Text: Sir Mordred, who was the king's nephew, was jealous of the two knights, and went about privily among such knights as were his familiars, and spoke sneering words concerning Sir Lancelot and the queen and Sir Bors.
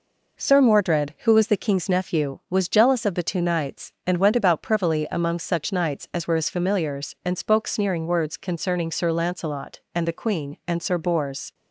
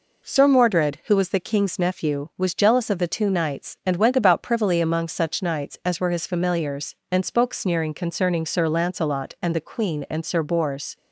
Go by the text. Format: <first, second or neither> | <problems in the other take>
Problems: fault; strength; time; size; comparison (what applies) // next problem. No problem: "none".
first | skips "words"; at 7.9 s